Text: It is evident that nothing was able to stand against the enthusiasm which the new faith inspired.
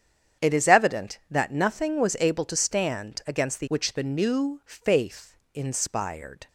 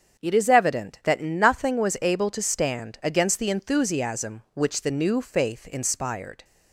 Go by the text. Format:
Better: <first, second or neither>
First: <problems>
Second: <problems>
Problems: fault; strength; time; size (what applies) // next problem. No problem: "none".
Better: second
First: starts louder than the rest; strong; until 1.5 s; 8.5 dB // skips "enthusiasm"; at 3.6 s // pauses between "faith" and "inspired"; slight; at 5.3 s; 0.20 s long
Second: starts louder than the rest; strong; until 1.2 s; 7.5 dB